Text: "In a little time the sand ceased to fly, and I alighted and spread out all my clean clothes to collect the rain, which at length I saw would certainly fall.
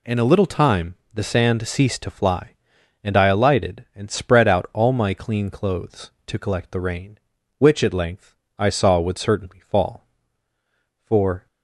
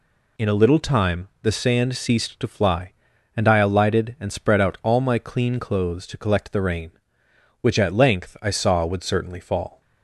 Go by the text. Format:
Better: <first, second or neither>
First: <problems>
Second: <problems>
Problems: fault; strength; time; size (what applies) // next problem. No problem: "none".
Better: second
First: pauses between "time" and "the"; slight; at 0.9 s; 0.18 s long // pauses between "length" and "I"; slight; at 8.3 s; 0.24 s long // goes on to say "For"; slight; from 11.0 s on; 0.40 s long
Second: none